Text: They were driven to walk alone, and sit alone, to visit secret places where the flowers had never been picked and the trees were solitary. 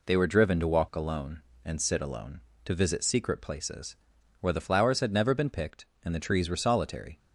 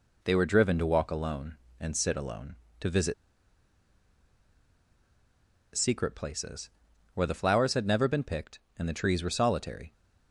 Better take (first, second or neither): first